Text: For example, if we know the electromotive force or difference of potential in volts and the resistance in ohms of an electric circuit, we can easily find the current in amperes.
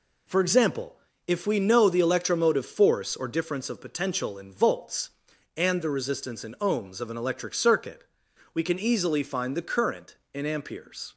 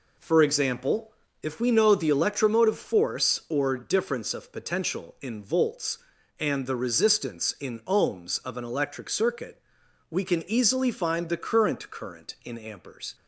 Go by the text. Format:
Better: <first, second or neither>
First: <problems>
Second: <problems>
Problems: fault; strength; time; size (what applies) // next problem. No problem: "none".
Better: first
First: none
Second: says "current" twice; at 11.8 s